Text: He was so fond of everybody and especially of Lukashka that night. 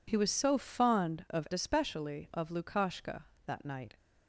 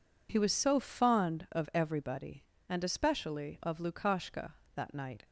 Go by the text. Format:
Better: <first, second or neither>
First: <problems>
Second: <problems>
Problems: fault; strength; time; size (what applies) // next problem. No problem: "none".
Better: second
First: skips "everybody and"; at 1.5 s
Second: none